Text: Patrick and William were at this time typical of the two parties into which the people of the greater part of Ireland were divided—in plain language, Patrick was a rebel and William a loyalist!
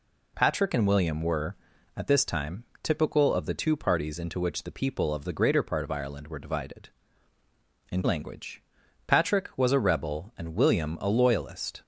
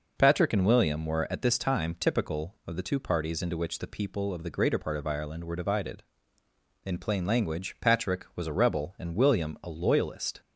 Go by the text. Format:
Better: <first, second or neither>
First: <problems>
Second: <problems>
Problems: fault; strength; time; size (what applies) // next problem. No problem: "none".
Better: second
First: pauses between "time" and "typical"; slight; at 2.6 s; 0.18 s long // skips "plain"; at 8.0 s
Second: none